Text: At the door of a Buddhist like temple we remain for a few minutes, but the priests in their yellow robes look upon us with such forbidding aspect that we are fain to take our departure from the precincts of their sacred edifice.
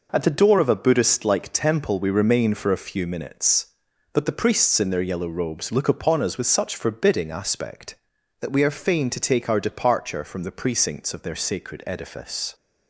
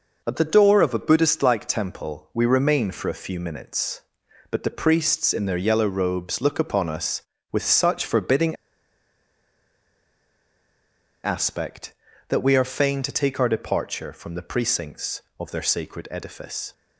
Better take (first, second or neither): first